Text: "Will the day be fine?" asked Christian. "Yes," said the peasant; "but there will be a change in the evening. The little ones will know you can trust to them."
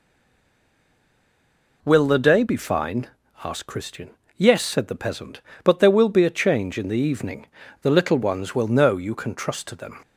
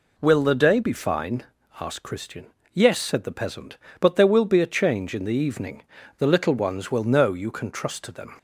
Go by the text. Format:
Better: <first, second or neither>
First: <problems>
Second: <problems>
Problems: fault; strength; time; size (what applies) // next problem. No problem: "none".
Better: second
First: stays silent before the first word; noticeable; until 1.8 s; 1.8 s long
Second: none